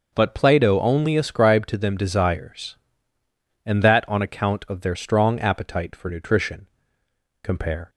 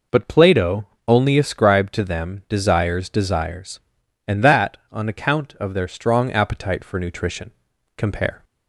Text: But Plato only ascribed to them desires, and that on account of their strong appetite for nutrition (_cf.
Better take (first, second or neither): first